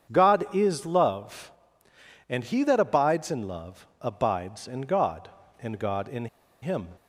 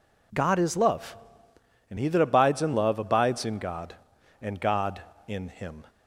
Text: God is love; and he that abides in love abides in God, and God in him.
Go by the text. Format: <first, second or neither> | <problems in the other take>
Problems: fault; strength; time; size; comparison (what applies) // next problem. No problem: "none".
second | starts louder than the rest; strong; until 1.1 s; 8 dB // pauses between "in" and "him"; slight; at 6.2 s; 0.35 s long